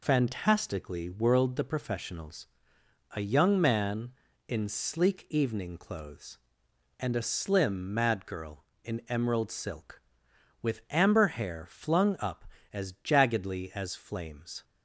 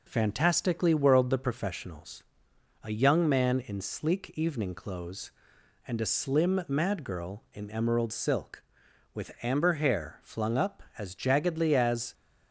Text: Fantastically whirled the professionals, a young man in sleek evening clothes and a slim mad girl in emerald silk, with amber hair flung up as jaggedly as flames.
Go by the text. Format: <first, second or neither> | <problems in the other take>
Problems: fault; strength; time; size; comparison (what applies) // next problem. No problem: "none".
first | stops before "flames"; at 12.1 s